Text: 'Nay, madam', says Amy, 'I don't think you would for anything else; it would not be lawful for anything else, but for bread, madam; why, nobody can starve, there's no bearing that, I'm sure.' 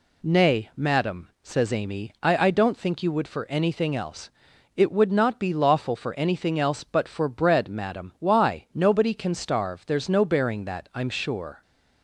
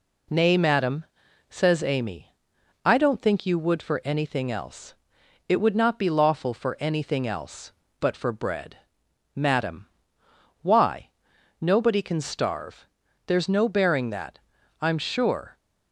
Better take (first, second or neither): second